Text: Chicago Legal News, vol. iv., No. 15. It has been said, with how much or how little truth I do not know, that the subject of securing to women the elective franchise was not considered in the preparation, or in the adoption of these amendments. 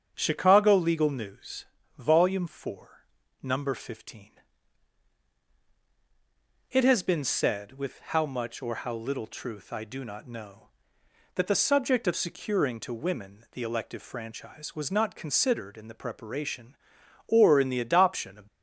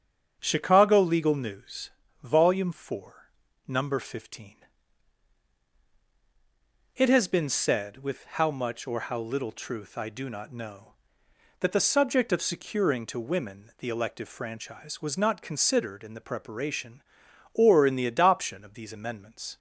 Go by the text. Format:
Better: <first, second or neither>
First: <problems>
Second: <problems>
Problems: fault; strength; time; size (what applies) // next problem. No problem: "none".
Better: second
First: starts louder than the rest; strong; until 1.1 s; 7.5 dB // stops before "these amendments"; at 18.4 s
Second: starts louder than the rest; strong; until 1.4 s; 7.5 dB